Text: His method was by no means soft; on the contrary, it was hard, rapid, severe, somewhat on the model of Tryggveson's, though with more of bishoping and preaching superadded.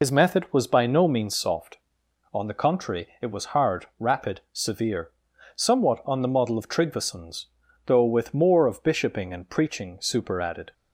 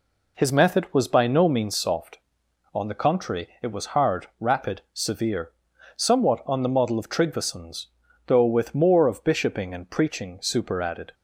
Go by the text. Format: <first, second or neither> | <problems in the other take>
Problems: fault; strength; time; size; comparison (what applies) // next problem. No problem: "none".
second | loses the start of "His"; at 0.0 s; 60 ms